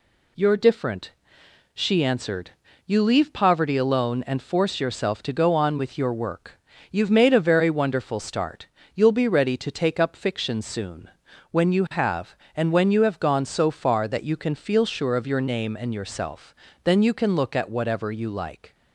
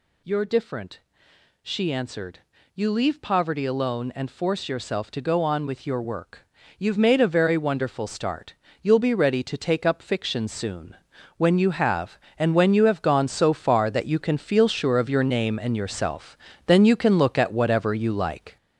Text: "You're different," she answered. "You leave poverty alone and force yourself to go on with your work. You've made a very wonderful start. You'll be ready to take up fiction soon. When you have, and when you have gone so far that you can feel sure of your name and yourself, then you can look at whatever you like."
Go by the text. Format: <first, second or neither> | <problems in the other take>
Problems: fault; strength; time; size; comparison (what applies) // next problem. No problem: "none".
first | gets louder; noticeable; throughout; 5 dB